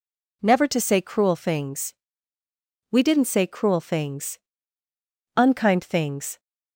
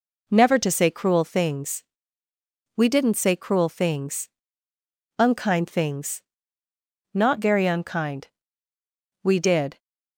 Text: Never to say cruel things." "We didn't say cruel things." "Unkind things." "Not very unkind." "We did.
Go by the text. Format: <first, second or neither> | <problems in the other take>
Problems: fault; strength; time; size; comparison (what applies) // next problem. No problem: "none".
second | stops before "Not very unkind We did"; at 6.3 s